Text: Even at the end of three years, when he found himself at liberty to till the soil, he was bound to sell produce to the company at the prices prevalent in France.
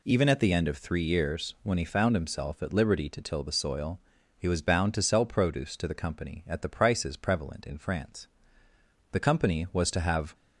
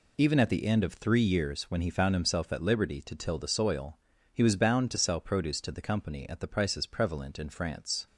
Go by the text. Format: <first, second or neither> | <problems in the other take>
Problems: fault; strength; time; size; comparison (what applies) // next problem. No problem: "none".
second | goes on to say "The company was to have"; noticeable; from 9.1 s on; 1.2 s long